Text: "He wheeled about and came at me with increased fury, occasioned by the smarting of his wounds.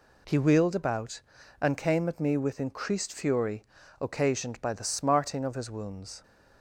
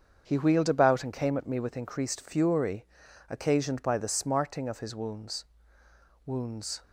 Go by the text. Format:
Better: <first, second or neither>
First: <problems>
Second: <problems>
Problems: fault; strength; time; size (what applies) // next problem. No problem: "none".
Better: first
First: none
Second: starts louder than the rest; strong; until 1.2 s; 7 dB // says "wounds" twice; at 6.2 s